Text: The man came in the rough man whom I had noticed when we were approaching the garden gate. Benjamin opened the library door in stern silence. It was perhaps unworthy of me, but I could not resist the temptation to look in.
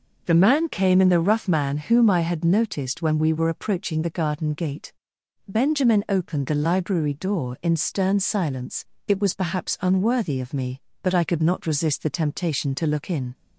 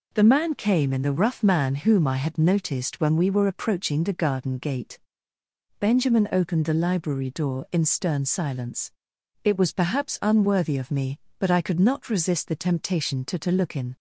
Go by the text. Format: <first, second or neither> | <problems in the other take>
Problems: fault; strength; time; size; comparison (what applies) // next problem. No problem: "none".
first | says "to" twice; at 13.3 s